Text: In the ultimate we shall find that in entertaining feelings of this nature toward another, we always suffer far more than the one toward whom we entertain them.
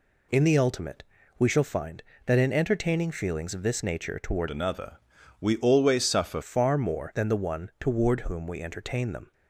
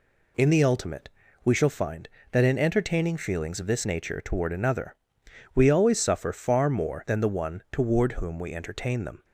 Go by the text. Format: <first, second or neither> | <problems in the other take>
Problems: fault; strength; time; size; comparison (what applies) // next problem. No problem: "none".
second | pauses between "ultimate" and "we"; slight; at 1.0 s; 0.34 s long; slight in the second // changes voice from "another" to "suffer"; from 4.4 to 6.4 s; 2.0 s long